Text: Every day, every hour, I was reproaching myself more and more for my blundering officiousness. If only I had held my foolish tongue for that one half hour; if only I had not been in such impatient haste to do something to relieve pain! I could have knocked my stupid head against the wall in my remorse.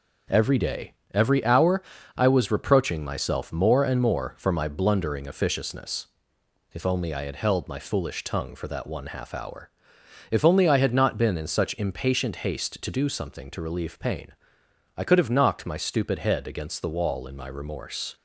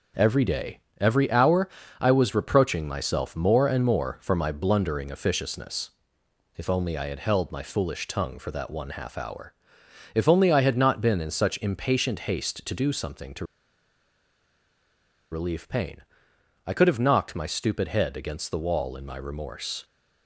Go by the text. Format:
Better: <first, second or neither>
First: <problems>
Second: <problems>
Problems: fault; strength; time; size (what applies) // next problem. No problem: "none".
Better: first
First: starts louder than the rest; noticeable; until 1.5 s; 6 dB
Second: starts louder than the rest; noticeable; until 1.4 s; 6 dB // pauses between "to" and "relieve"; strong; at 13.4 s; 1.8 s long